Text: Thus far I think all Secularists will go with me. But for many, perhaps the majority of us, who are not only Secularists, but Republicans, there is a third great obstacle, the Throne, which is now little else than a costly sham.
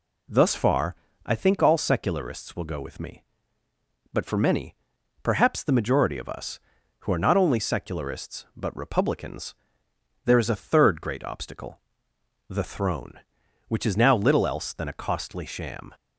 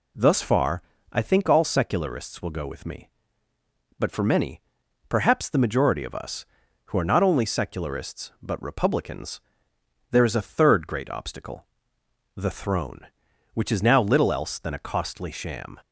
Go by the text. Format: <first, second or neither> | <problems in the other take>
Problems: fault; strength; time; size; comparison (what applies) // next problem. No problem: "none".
neither | pauses between "far" and "I"; slight; the same in both